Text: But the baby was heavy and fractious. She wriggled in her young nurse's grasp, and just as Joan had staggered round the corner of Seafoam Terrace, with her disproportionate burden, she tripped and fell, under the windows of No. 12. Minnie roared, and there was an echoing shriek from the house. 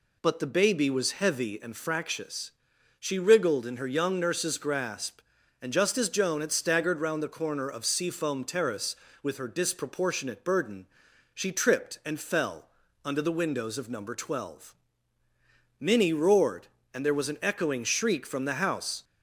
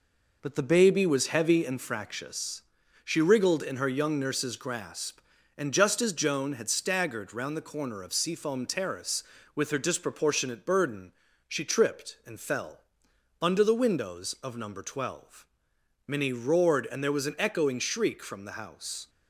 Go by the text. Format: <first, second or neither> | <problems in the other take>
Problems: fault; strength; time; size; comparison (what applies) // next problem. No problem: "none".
first | gets quieter; noticeable; throughout; 5 dB